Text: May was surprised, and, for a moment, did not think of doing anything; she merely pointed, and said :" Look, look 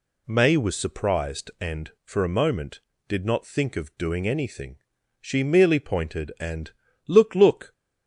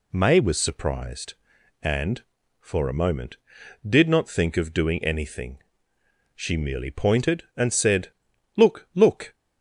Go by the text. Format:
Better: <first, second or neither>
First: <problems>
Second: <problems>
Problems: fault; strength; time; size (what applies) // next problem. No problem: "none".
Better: second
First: skips "said"; at 6.8 s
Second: none